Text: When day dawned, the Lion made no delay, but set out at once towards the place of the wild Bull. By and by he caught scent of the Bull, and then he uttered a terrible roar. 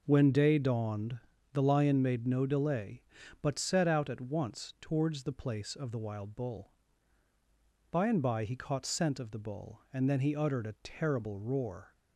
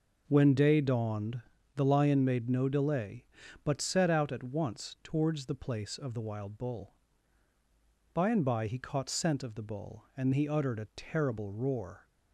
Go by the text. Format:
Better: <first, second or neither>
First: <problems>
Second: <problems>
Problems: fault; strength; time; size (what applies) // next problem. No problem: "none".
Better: first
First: none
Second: skips "then"; at 10.3 s